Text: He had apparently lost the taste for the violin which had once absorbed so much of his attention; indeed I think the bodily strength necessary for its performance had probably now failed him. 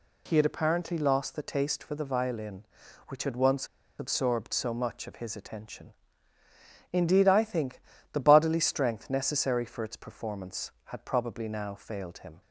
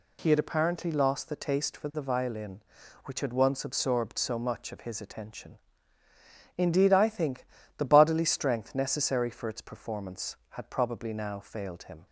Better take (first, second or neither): second